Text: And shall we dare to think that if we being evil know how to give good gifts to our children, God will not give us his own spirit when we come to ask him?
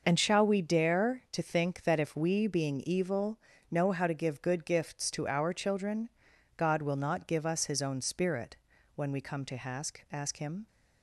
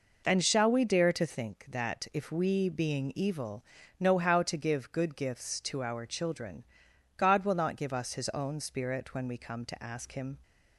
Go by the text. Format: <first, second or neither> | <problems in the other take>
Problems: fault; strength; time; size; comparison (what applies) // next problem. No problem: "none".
second | pauses between "evil" and "know"; slight; at 3.3 s; 0.32 s long; slight in the second // pauses between "spirit" and "when"; at 8.5 s; 0.38 s long // says "ask" twice; at 10.1 s